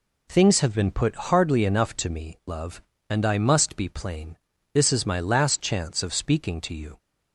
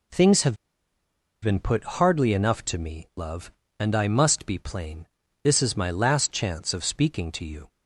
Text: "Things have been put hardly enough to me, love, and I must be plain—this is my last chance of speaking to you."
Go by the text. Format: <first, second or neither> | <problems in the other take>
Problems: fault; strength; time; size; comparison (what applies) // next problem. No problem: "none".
first | pauses between "have" and "been"; noticeable; at 0.5 s; 0.86 s long